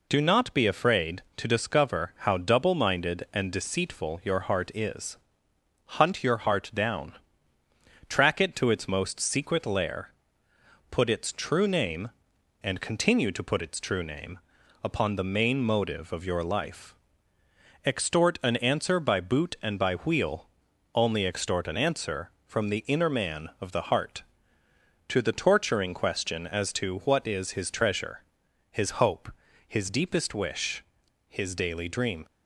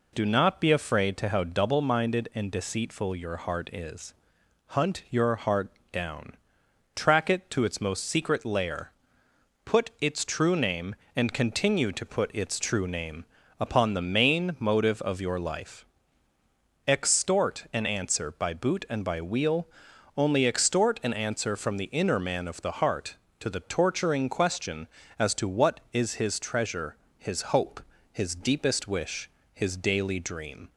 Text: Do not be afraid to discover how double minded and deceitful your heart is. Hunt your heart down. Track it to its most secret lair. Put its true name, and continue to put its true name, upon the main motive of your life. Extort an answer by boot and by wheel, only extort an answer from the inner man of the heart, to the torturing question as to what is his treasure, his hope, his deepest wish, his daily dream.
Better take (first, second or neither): first